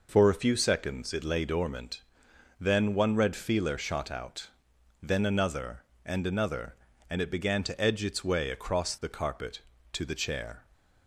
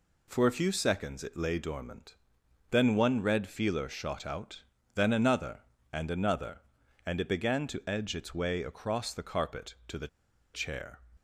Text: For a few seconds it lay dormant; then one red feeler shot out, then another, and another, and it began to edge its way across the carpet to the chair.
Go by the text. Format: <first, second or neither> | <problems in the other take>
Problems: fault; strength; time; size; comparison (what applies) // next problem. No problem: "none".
first | pauses between "the" and "chair"; noticeable; at 10.0 s; 0.46 s long